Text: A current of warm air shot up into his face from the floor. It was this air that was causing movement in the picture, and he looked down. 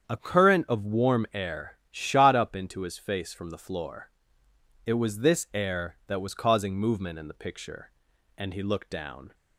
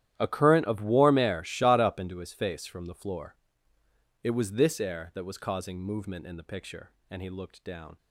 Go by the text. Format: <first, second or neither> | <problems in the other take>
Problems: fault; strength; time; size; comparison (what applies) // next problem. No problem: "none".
first | gets quieter; strong; throughout; 17.5 dB // starts louder than the rest; strong; until 1.1 s; 11.5 dB; strong in the first